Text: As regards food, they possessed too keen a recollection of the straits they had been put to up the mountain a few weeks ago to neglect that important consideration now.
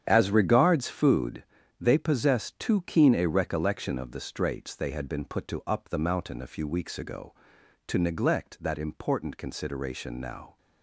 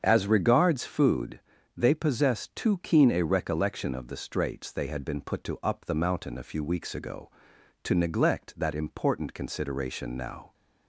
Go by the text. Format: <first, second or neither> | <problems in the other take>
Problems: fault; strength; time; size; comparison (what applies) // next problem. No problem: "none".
second | gets quieter; strong; throughout; 10.5 dB // starts louder than the rest; strong; until 1.0 s; 9 dB; strong in the second